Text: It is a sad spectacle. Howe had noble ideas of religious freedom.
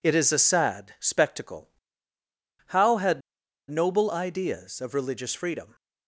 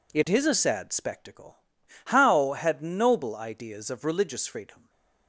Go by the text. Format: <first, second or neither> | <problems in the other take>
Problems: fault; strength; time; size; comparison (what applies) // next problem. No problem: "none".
second | pauses between "had" and "noble"; noticeable; at 3.2 s; 0.50 s long